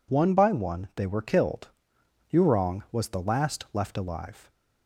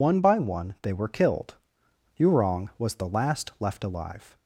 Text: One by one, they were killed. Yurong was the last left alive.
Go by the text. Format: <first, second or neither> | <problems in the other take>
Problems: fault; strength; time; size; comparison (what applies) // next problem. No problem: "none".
first | loses the start of "One"; at 0.0 s; 55 ms